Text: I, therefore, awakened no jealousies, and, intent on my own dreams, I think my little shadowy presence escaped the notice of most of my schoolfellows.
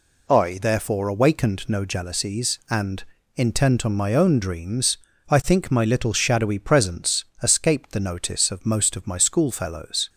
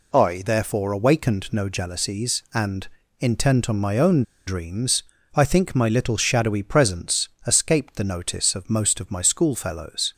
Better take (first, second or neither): first